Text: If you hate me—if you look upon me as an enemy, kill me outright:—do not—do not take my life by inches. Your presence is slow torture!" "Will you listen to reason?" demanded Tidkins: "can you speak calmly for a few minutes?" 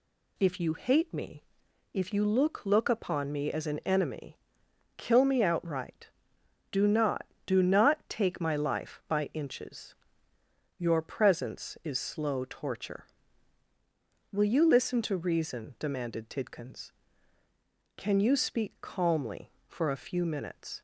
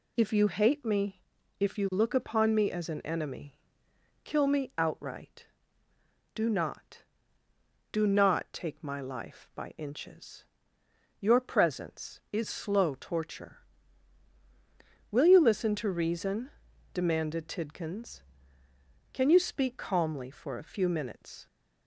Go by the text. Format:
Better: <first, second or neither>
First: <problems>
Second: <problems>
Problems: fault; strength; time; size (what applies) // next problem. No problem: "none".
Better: second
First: says "look" twice; at 2.6 s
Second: none